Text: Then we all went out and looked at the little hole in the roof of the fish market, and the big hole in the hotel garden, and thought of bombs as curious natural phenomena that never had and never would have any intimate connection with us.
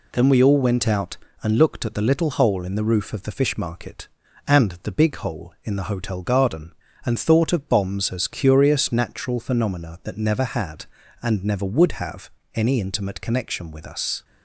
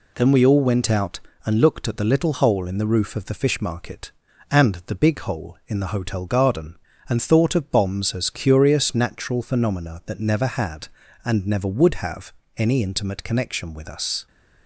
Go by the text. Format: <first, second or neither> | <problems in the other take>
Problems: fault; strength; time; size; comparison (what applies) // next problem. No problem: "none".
neither | pauses between "have" and "any"; slight; the same in both